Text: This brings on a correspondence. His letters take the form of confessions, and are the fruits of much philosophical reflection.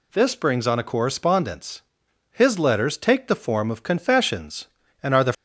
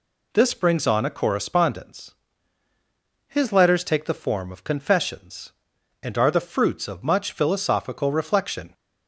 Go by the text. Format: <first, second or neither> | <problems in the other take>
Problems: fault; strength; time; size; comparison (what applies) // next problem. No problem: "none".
second | stops before "fruits of much philosophical reflection"; at 5.3 s